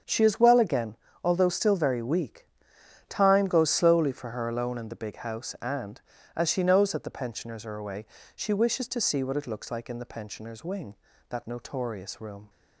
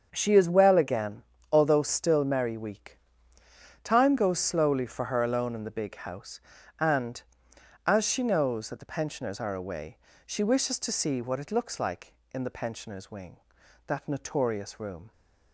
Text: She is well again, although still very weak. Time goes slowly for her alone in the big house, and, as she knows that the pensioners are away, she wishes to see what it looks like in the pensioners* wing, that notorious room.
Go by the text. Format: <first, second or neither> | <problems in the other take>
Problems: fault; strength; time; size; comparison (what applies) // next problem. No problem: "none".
first | starts louder than the rest; until 1.1 s; 7 dB; strong in the first // says "merry" for "very"; at 2.2 s